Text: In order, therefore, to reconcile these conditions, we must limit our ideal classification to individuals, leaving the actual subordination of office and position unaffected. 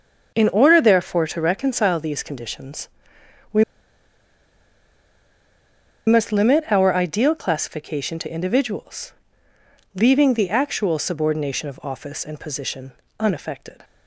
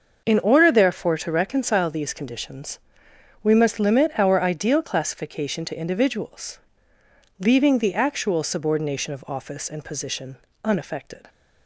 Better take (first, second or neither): second